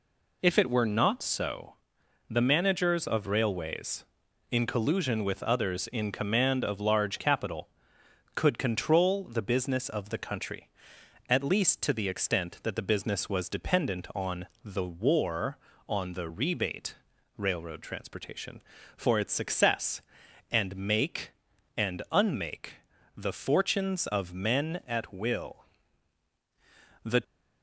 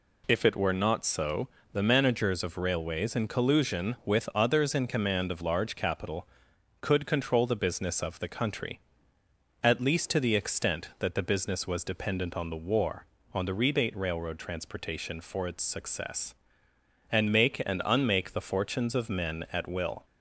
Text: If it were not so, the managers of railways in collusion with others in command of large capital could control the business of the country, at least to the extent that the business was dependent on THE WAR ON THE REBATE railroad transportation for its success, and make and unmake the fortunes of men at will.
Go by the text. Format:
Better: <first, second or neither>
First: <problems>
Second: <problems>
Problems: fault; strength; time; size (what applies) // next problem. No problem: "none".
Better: second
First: pauses between "on" and "THE"; slight; at 14.4 s; 0.18 s long // pauses between "REBATE" and "railroad"; at 16.9 s; 0.42 s long // pauses between "unmake" and "the"; at 22.7 s; 0.42 s long // goes on to say "The"; slight; from 27.0 s on; 0.18 s long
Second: none